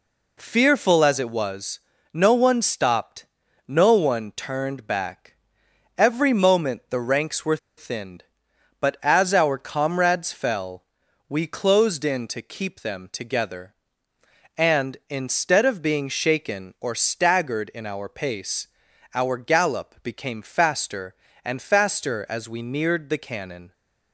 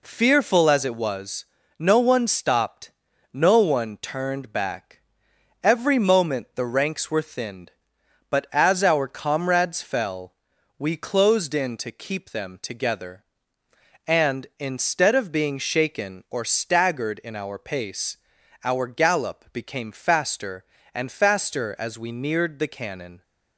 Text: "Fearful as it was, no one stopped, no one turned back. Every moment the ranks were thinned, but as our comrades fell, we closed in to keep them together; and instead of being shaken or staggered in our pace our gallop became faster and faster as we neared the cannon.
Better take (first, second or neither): second